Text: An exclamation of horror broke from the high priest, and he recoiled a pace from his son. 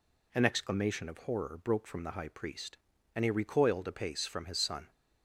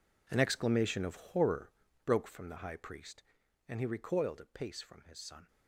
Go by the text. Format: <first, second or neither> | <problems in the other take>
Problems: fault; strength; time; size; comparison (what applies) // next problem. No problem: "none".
first | gets quieter; strong; throughout; 15 dB // pauses between "horror" and "broke"; slight; at 1.7 s; 0.34 s long